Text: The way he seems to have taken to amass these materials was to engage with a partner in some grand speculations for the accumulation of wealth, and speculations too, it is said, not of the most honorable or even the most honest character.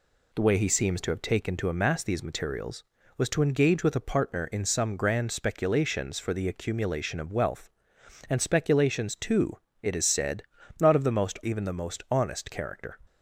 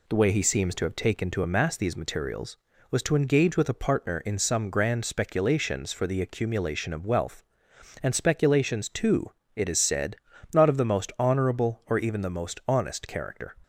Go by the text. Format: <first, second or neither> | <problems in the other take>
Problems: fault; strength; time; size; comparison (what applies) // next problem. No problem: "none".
second | skips "honorable or"; at 11.4 s